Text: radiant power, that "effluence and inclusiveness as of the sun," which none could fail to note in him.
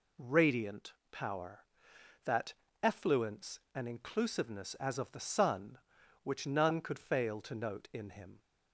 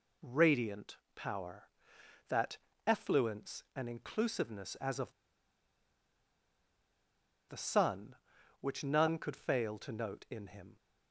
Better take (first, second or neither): first